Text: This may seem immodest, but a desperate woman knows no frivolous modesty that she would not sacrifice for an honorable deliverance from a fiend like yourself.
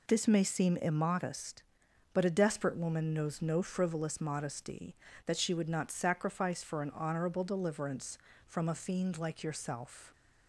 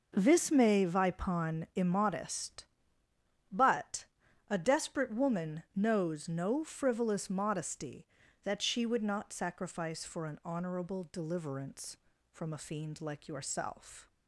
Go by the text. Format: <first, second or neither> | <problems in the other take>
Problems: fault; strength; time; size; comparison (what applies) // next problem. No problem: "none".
first | says "vipon" for "seem"; at 0.8 s // pauses between "but" and "a"; at 4.0 s; 0.42 s long